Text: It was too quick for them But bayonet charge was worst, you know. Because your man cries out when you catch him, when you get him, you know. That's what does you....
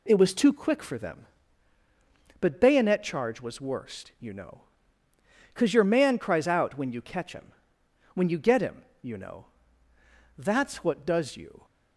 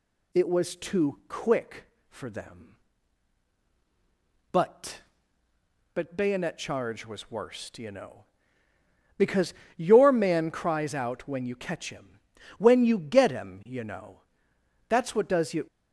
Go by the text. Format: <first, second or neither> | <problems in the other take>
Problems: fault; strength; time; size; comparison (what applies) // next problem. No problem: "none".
first | says "But" twice; at 5.9 s // pauses between "Because" and "your"; slight; at 9.5 s; 0.22 s long